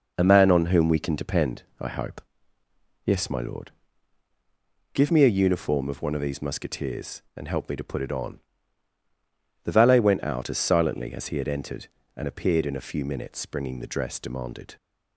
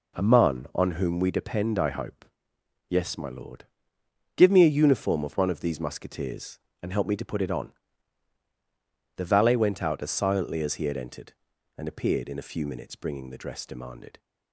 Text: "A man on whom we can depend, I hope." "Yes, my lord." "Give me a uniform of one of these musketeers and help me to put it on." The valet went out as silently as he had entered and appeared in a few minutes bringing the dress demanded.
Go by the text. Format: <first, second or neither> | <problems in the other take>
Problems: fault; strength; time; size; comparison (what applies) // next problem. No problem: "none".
first | skips "can"; at 1.3 s